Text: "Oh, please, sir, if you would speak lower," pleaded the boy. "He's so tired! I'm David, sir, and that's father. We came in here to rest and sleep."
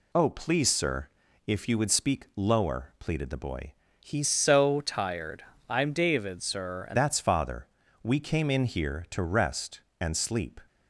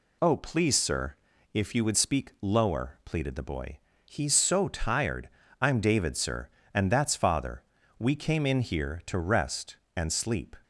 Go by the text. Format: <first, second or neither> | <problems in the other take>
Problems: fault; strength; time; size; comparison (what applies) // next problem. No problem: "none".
second | changes voice from "so" to "and"; from 4.2 to 6.9 s; 2.7 s long